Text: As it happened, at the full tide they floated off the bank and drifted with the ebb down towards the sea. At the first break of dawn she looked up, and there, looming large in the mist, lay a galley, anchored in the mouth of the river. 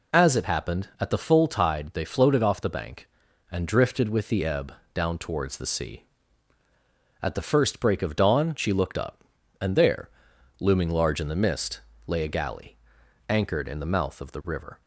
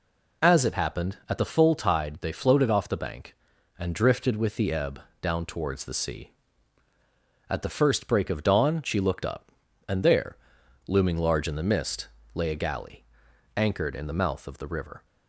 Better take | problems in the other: neither | pauses between "ebb" and "down"; slight; the same in both

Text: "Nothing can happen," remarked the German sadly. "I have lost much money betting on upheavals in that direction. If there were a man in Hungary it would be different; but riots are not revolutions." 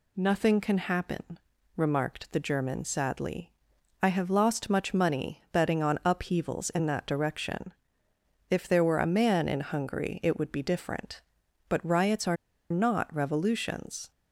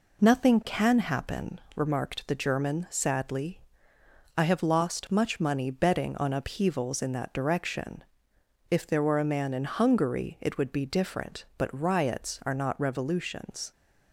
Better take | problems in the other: second | pauses between "are" and "not"; at 12.3 s; 0.36 s long

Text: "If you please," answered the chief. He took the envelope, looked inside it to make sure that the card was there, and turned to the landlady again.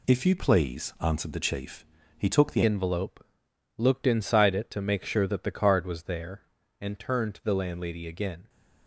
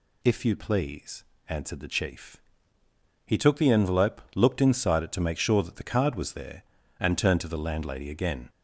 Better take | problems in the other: second | changes voice at "envelope"; from 2.6 s on; 5.8 s long

